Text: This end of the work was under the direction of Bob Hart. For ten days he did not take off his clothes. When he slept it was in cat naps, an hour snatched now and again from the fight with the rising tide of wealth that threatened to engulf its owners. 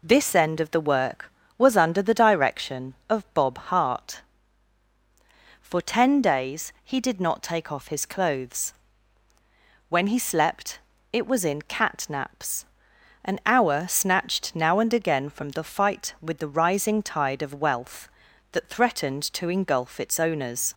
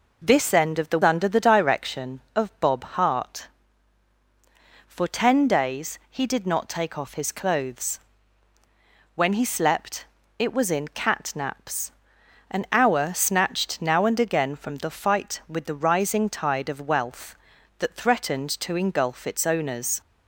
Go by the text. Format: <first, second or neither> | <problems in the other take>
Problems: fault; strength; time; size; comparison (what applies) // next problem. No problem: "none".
first | skips "work was"; at 1.0 s // pauses between "slept" and "it"; slight; at 10.0 s; 0.32 s long; slight in the first